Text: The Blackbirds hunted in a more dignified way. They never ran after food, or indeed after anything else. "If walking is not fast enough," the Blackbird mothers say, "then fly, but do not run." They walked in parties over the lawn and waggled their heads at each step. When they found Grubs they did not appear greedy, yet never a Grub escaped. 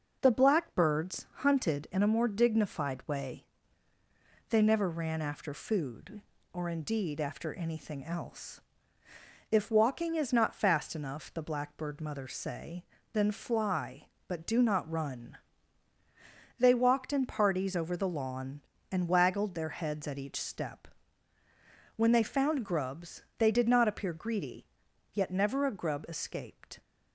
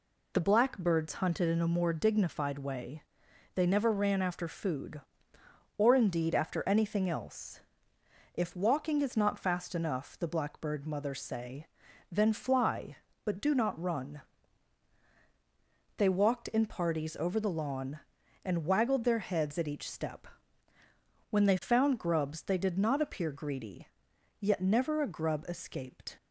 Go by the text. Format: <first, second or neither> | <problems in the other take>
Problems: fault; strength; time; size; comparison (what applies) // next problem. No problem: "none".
neither | none